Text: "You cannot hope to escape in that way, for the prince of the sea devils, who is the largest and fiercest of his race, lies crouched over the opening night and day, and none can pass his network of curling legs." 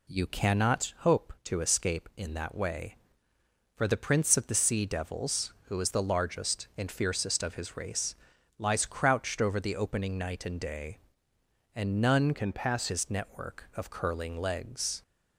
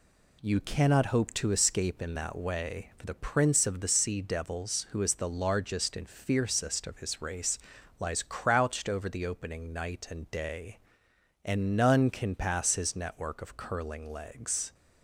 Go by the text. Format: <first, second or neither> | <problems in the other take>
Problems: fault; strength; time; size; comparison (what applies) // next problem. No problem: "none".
second | changes voice from "can" to "pass"; from 12.3 to 12.8 s; 0.5 s long